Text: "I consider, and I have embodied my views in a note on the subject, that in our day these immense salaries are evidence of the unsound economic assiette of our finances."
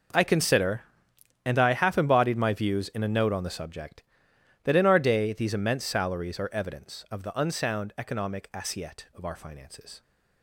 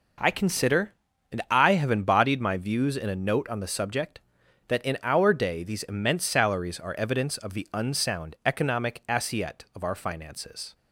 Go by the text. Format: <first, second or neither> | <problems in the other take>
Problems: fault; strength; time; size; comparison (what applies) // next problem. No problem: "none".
second | says "half" for "have"; at 1.7 s